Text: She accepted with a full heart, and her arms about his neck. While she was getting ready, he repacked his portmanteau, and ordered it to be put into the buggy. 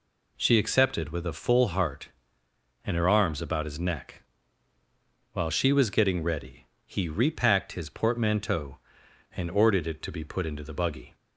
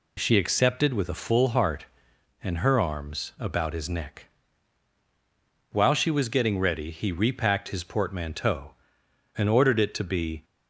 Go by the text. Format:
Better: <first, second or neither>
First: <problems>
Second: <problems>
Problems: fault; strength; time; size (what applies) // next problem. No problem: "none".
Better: first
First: none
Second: stops before "put into the buggy"; at 10.4 s